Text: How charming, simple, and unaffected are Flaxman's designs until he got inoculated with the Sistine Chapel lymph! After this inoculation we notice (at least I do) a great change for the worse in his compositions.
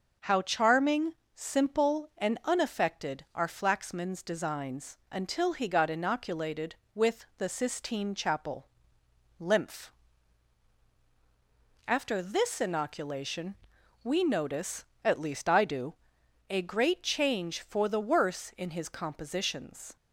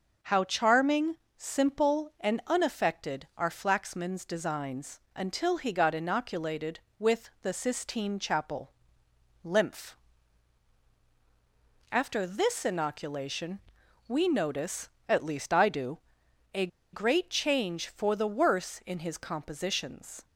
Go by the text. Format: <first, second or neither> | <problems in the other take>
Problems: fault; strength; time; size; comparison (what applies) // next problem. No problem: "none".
first | pauses between "designs" and "until"; slight; at 4.9 s; 0.16 s long // pauses between "Chapel" and "lymph"; noticeable; at 8.7 s; 0.72 s long; noticeable in the first // pauses between "inoculation" and "we"; noticeable; at 13.5 s; 0.48 s long; noticeable in the first // pauses between "a" and "great"; slight; at 16.6 s; 0.25 s long